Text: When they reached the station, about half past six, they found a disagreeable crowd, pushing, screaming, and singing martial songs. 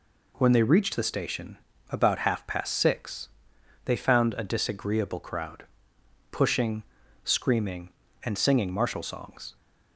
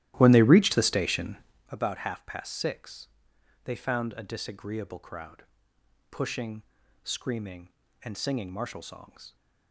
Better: first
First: none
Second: starts louder than the rest; strong; until 1.7 s; 14.5 dB

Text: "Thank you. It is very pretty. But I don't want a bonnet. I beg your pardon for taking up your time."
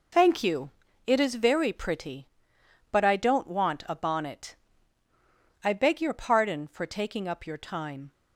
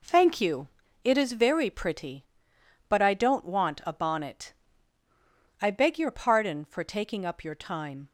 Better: second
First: loses the start of "Thank"; at 0.1 s; 75 ms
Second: none

